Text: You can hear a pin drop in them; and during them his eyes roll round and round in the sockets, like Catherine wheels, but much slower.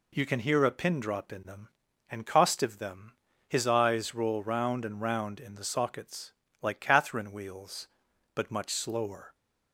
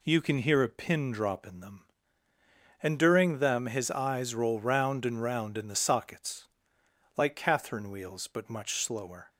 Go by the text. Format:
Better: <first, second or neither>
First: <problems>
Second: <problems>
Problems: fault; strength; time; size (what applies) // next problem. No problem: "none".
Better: second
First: says "costive" for "during"; at 2.2 s // pauses between "them" and "his"; slight; at 3.1 s; 0.34 s long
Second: none